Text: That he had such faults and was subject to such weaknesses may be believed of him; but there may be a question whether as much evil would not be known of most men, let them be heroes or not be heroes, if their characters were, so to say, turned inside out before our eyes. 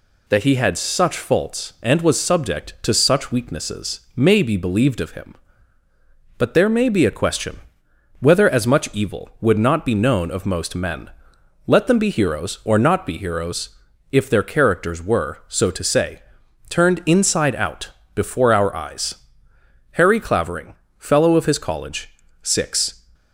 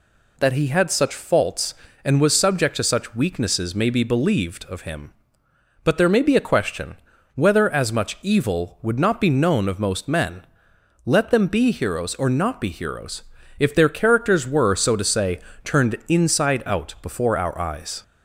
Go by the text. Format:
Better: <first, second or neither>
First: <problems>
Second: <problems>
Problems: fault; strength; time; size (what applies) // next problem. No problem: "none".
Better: second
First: pauses between "weaknesses" and "may"; slight; at 4.0 s; 0.16 s long // pauses between "question" and "whether"; noticeable; at 7.6 s; 0.58 s long // pauses between "out" and "before"; slight; at 17.9 s; 0.24 s long // goes on to say "Harry Clavering fellow of his college six"; strong; from 19.9 s on; 3.1 s long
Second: pauses between "question" and "whether"; at 6.9 s; 0.38 s long